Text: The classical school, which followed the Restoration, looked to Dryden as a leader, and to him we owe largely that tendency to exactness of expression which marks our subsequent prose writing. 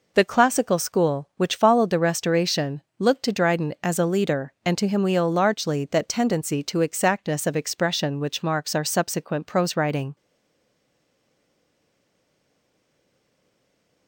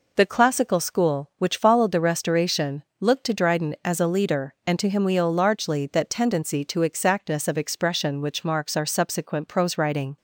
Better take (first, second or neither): second